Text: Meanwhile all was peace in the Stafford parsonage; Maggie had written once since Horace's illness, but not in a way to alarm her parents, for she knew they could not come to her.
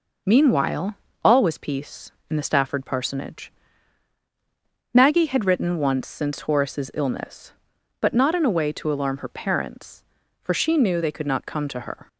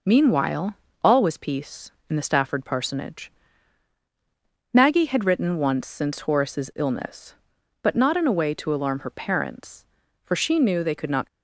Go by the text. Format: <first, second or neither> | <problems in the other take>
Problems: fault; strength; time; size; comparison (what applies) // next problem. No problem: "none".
first | pauses between "Meanwhile" and "all"; slight; at 0.7 s; 0.30 s long; slight in the first // stops before "come to her"; at 11.2 s